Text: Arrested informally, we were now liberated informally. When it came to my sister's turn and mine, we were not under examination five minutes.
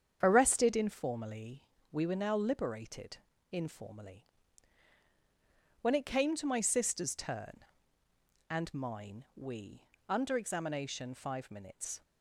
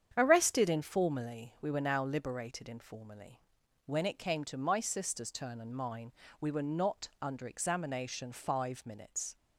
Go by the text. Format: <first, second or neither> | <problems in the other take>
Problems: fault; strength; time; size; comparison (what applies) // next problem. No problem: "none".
second | starts louder than the rest; strong; until 1.2 s; 8 dB; strong in the second // pauses between "liberated" and "informally"; slight; at 3.1 s; 0.34 s long // skips "were not"; at 9.9 s